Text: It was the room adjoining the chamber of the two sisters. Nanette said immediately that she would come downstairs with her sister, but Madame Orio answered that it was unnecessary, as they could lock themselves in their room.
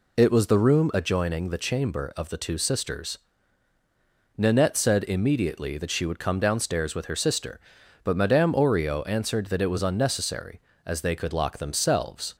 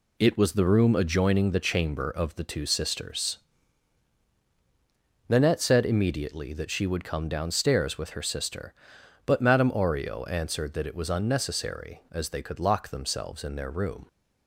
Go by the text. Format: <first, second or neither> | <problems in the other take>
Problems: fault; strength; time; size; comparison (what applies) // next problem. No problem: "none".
second | stops before "in their room"; at 12.3 s